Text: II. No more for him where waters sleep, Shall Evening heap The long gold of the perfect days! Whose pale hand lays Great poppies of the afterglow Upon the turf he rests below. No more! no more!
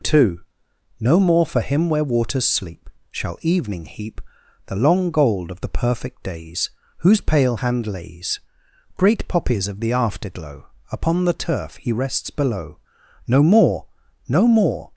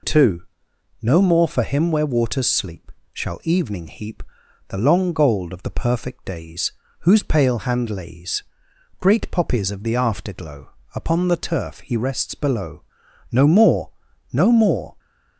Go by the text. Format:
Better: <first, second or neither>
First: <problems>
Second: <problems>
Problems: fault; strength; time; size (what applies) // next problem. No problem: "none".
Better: neither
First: pauses between "heap" and "The"; noticeable; at 4.2 s; 0.46 s long // pauses between "lays" and "Great"; noticeable; at 8.4 s; 0.56 s long // pauses between "afterglow" and "Upon"; slight; at 10.6 s; 0.24 s long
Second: pauses between "heap" and "The"; noticeable; at 4.2 s; 0.46 s long // pauses between "lays" and "Great"; noticeable; at 8.4 s; 0.56 s long // pauses between "afterglow" and "Upon"; slight; at 10.6 s; 0.24 s long